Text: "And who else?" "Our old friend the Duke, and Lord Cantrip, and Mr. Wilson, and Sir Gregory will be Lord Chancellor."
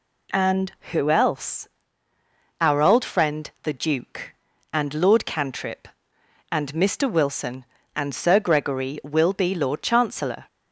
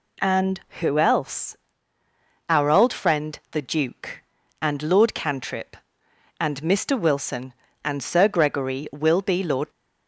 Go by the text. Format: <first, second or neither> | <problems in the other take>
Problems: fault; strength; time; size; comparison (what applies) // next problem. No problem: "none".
first | stops before "Chancellor"; at 9.7 s